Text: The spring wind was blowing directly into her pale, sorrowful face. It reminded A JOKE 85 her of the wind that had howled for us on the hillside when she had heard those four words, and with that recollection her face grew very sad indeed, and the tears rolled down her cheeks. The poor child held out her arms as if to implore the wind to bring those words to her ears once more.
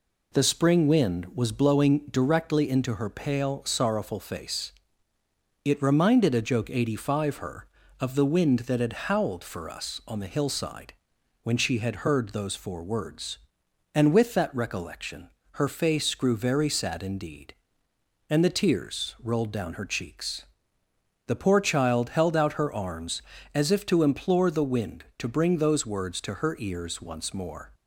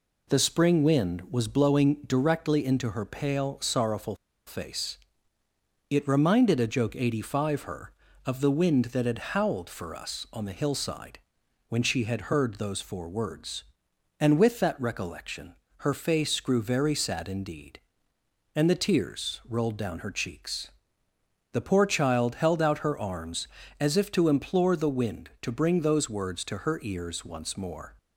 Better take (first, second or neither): first